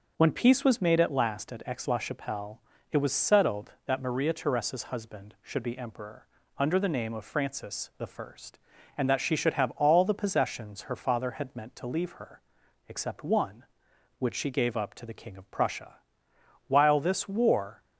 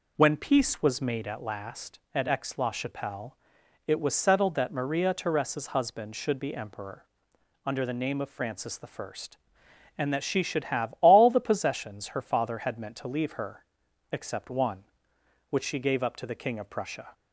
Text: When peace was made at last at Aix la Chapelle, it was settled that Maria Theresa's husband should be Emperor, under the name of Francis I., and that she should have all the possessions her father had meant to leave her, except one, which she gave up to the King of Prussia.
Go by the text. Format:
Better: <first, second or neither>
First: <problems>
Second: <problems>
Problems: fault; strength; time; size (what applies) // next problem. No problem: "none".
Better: second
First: goes on to say "While this war"; noticeable; from 16.6 s on; 1.1 s long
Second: none